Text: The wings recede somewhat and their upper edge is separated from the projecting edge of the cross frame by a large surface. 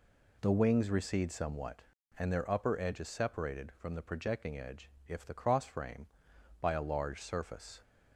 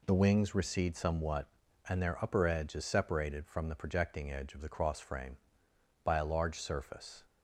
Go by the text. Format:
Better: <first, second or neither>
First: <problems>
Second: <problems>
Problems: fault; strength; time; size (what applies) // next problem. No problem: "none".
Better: second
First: says "if" for "of"; at 5.0 s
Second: none